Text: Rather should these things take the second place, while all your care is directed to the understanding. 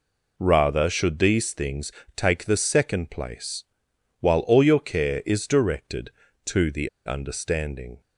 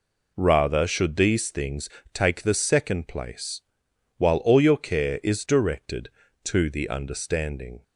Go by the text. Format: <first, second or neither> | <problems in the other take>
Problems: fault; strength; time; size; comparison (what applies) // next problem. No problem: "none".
second | pauses between "things" and "take"; slight; at 1.9 s; 0.24 s long; slight in the second // pauses between "the" and "understanding"; slight; at 6.8 s; 0.17 s long